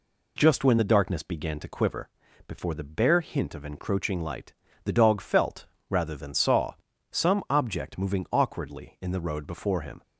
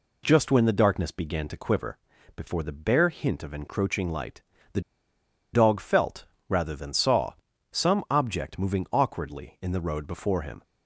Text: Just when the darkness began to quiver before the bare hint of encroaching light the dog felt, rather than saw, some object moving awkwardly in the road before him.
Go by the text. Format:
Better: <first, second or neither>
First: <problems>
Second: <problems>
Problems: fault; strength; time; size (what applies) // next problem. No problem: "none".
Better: first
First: pauses between "quiver" and "before"; slight; at 2.0 s; 0.36 s long // pauses between "light" and "the"; slight; at 4.5 s; 0.32 s long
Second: pauses between "quiver" and "before"; slight; at 1.9 s; 0.36 s long // pauses between "light" and "the"; slight; at 4.4 s; 0.32 s long // pauses between "the" and "dog"; noticeable; at 4.8 s; 0.73 s long